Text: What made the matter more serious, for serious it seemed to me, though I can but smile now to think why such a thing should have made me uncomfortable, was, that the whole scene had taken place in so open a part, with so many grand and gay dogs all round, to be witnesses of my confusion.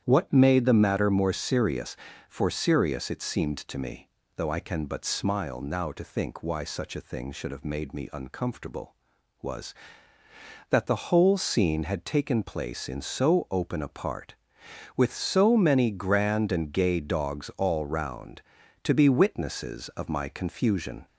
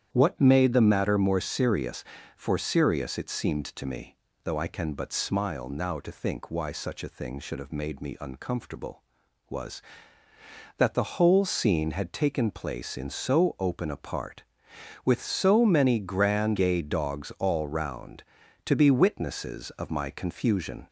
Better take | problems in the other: first | starts louder than the rest; strong; until 1.1 s; 9.5 dB; strong in the first // skips "and"; at 16.5 s

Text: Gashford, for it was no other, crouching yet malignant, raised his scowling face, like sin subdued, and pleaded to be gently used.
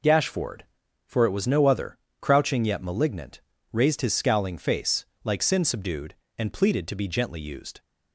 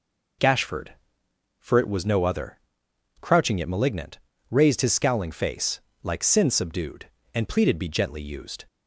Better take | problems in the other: first | skips "to"; at 7.7 s

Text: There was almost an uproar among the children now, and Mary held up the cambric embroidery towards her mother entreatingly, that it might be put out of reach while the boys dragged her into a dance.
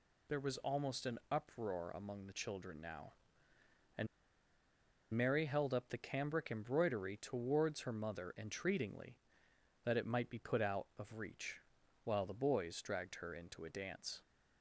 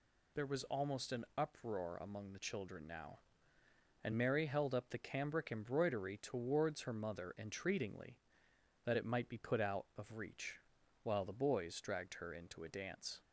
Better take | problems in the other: second | pauses between "and" and "Mary"; at 4.0 s; 1.0 s long // pauses between "reach" and "while"; at 11.6 s; 0.44 s long; also in the second

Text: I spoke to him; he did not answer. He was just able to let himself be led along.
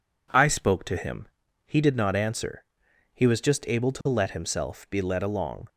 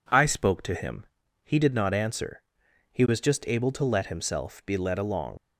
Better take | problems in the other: first | leaves "along" unfinished; at 5.3 s; 65 ms

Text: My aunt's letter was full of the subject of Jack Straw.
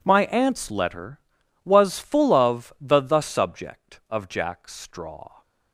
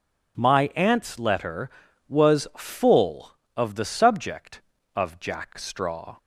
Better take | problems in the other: second | says "the" twice; at 3.0 s

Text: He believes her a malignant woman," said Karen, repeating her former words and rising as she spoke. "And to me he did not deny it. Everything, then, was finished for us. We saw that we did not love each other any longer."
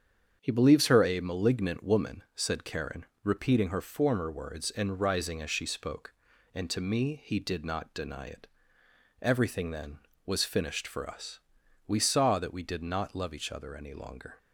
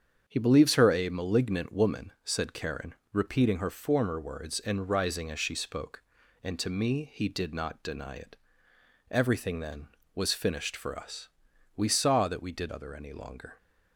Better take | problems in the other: first | starts louder than the rest; strong; until 1.2 s; 7.5 dB; strong in the first // skips "not love each"; at 12.7 s

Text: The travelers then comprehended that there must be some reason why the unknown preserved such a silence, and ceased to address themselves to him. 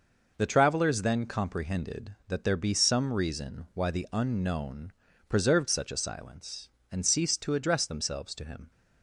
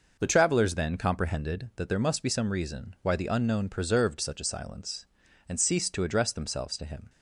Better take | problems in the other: second | skips "must"; at 2.5 s // pauses between "unknown" and "preserved"; slight; at 4.9 s; 0.36 s long

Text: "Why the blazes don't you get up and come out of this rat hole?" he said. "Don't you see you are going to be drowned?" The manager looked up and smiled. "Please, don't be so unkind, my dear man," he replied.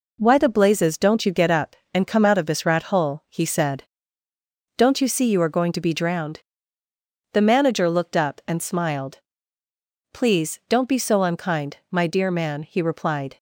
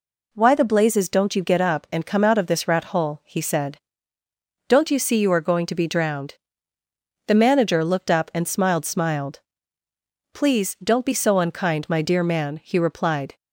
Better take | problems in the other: first | says "smiled" twice; at 8.8 s

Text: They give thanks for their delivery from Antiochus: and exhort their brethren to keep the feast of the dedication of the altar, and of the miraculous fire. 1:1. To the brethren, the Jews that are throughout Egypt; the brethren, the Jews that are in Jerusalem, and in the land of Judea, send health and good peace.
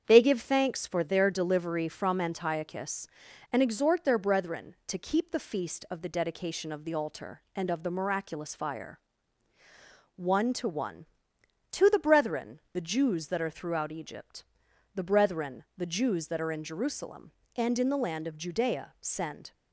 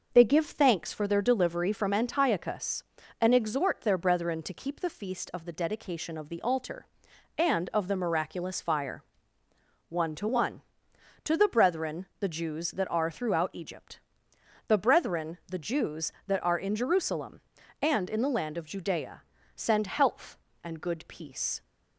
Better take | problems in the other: second | starts louder than the rest; strong; until 1.0 s; 7.5 dB // stops before "health and good peace"; at 19.5 s

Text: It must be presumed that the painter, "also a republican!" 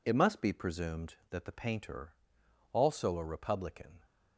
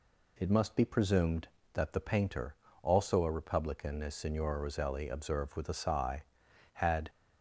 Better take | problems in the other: first | goes on to say "as Signora Roselli observed with a sigh had"; strong; from 4.0 s on; 3.0 s long

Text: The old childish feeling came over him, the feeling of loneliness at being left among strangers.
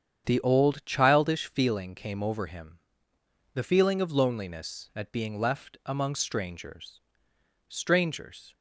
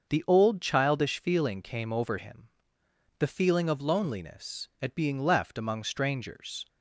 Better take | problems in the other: second | starts louder than the rest; strong; until 1.2 s; 8 dB; also in the second // says "strangers" twice; at 7.6 s

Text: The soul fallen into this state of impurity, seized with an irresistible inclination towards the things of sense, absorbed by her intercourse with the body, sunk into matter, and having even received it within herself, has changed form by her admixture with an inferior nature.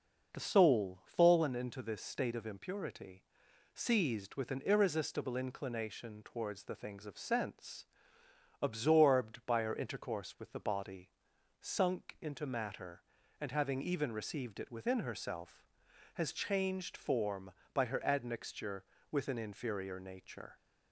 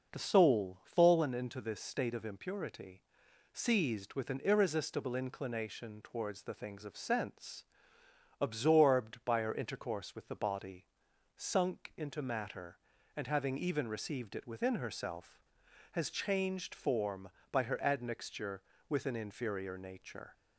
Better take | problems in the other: neither | none

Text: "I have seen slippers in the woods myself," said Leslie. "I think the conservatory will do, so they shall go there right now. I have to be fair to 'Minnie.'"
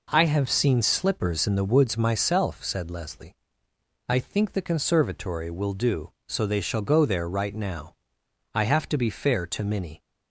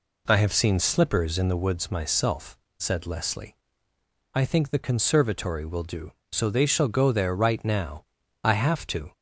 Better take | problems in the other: first | stops before "be fair to Minnie"; at 9.1 s

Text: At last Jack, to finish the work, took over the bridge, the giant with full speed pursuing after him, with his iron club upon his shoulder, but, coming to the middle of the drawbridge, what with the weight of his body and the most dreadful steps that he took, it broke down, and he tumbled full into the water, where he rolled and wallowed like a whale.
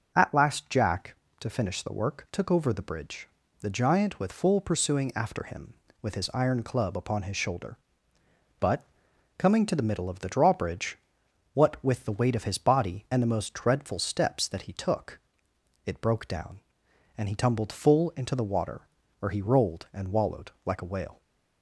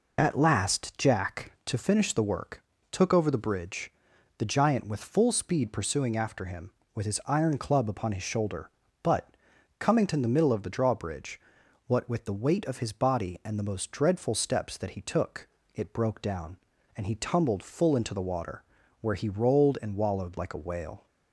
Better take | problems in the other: second | skips "speed"; at 4.6 s

